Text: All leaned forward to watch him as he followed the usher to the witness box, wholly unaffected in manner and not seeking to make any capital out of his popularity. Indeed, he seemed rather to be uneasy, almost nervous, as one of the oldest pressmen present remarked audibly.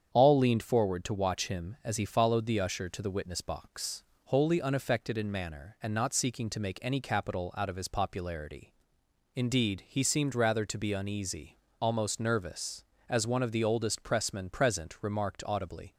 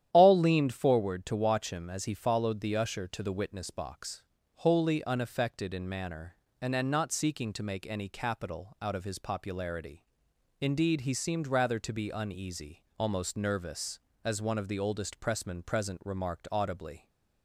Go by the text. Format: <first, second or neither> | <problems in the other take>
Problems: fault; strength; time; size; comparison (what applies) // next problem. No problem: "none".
first | starts louder than the rest; strong; until 1.1 s; 11 dB; strong in the first // says "and" twice; at 6.7 s